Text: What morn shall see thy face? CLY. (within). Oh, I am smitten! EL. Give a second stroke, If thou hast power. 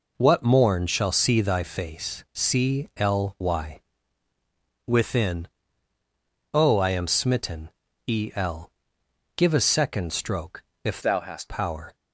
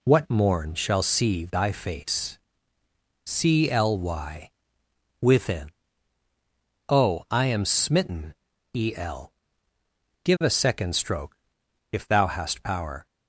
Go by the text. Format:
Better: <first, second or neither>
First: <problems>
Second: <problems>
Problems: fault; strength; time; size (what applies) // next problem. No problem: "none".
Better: second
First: changes voice from "thou" to "hast"; from 11.0 to 11.5 s; 0.5 s long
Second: none